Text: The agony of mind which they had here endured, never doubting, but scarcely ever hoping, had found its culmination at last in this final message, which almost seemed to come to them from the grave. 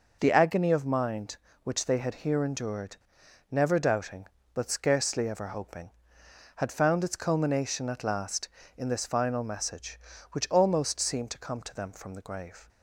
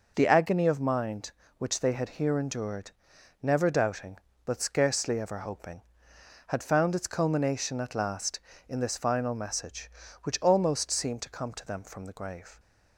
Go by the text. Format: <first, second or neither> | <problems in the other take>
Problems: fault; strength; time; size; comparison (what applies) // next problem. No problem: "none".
neither | none